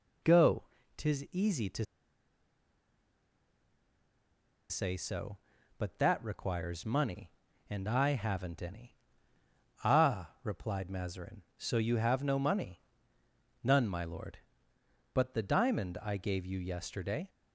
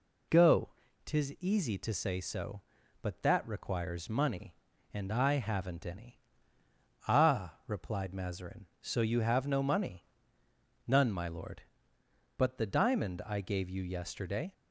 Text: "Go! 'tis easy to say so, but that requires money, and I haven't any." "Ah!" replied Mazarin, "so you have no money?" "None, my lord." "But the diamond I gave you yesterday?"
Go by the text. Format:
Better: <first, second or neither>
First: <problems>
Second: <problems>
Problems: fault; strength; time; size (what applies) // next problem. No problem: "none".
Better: second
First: pauses between "to" and "say"; strong; at 1.8 s; 2.8 s long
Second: none